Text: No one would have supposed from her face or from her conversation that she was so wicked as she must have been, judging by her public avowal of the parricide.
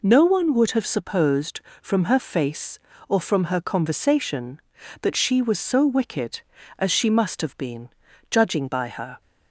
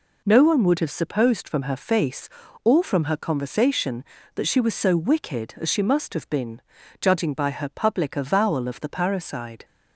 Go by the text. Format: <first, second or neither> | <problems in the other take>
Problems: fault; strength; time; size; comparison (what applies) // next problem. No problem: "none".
second | stops before "public avowal of the parricide"; at 9.2 s